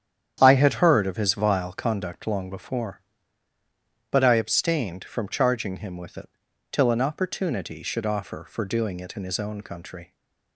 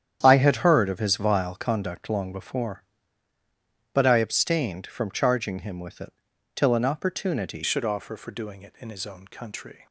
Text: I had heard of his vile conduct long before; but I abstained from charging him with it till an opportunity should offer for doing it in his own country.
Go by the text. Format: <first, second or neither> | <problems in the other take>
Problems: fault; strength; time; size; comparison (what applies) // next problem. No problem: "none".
first | starts louder than the rest; strong; until 1.2 s; 9.5 dB; strong in the first // pauses between "it" and "till"; at 6.1 s; 0.40 s long; also in the first // changes voice at "should"; from 7.6 s on; 2.2 s long